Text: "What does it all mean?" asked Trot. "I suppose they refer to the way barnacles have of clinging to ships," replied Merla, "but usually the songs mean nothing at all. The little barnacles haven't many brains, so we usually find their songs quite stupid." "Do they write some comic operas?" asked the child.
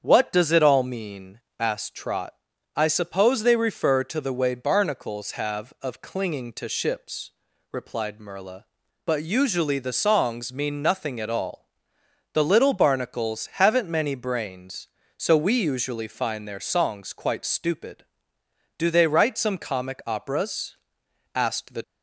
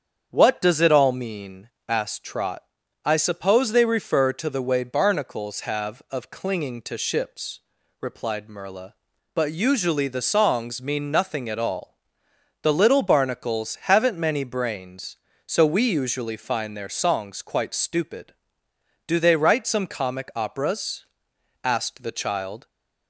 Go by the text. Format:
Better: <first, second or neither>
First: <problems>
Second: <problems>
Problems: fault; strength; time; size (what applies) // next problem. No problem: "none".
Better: second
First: starts louder than the rest; strong; until 1.0 s; 7.5 dB // stops before "child"; at 21.8 s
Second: starts louder than the rest; strong; until 1.3 s; 7.5 dB